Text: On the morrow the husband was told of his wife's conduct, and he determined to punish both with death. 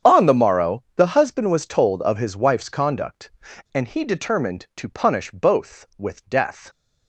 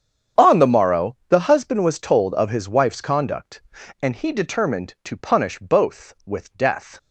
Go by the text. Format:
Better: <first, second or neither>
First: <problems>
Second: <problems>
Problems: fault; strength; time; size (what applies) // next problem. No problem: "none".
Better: neither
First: starts louder than the rest; strong; until 1.1 s; 8 dB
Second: starts louder than the rest; strong; until 1.5 s; 8 dB